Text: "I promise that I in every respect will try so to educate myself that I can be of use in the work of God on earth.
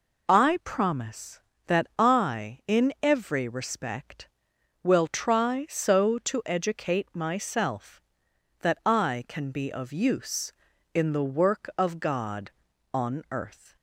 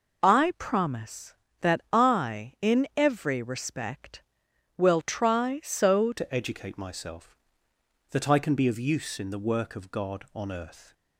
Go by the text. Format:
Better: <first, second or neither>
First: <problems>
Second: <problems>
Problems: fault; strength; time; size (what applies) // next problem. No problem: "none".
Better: first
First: none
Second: changes voice at "to"; from 6.1 s on; 4.8 s long